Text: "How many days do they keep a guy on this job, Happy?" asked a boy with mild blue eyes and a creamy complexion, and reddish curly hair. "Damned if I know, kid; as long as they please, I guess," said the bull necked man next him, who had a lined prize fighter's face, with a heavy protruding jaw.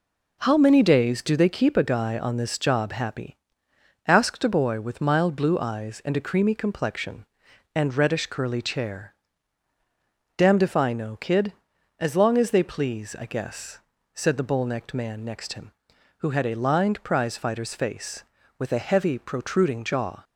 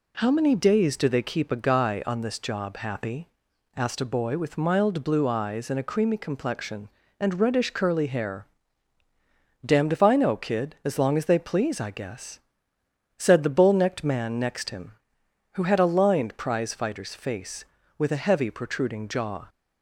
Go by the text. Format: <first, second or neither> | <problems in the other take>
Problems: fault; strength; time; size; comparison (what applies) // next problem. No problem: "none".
second | says "chair" for "hair"; at 8.6 s